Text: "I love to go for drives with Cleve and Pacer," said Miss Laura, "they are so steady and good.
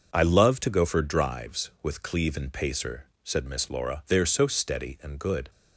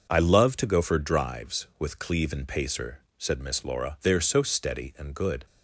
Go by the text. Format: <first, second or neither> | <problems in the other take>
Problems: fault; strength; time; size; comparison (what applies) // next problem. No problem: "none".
neither | none